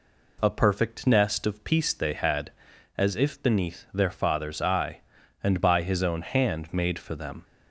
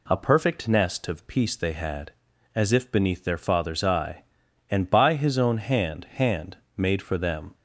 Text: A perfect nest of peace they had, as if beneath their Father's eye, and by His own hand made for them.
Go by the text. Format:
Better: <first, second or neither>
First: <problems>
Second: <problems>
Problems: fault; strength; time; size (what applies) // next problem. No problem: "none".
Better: first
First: none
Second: says "hand" twice; at 6.1 s